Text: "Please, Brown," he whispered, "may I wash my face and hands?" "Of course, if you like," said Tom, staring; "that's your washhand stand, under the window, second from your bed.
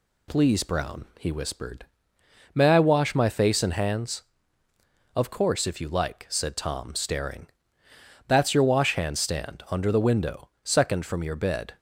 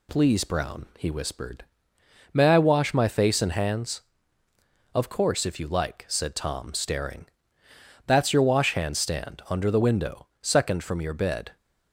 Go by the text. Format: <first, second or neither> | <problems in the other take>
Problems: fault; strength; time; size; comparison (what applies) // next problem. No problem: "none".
neither | none